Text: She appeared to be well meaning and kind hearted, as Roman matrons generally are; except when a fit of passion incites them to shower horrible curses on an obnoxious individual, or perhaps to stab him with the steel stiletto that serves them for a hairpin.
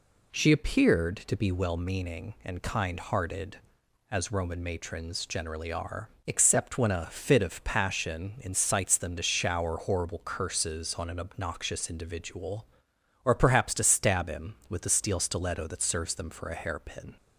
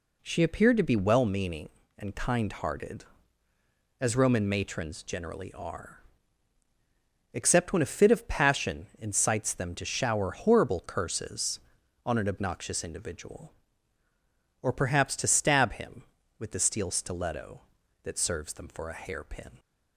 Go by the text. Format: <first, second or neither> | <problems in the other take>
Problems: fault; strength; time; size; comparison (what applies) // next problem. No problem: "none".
neither | none